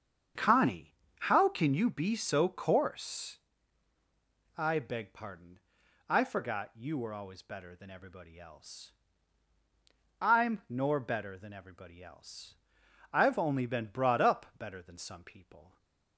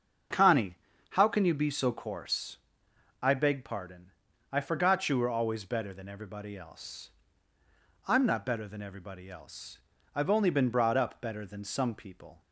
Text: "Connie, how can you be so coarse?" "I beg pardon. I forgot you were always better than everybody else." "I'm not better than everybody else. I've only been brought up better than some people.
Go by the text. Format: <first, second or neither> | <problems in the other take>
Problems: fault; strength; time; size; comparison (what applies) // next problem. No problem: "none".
second | starts louder than the rest; strong; until 1.6 s; 7.5 dB; also in the second // says "nor" for "not"; at 10.6 s